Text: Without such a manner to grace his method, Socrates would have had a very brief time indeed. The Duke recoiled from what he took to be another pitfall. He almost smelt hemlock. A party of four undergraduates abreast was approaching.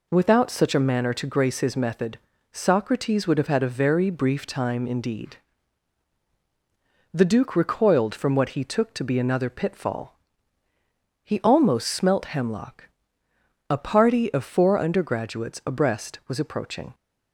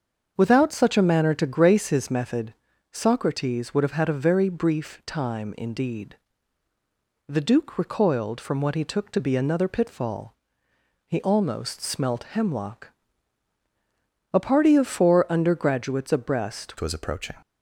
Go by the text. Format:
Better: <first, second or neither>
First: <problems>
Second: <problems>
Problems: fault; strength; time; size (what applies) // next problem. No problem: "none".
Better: first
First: none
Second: starts louder than the rest; until 1.3 s; 6.5 dB // changes voice at "was"; from 16.7 s on; 0.6 s long